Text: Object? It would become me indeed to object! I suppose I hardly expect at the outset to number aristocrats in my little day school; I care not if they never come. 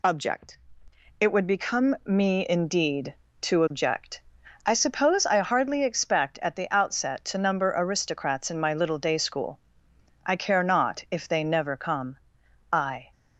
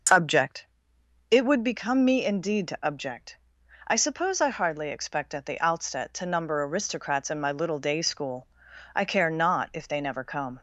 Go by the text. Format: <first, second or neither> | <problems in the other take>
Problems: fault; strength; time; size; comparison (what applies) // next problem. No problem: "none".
second | goes on to say "I"; slight; from 12.7 s on; 0.38 s long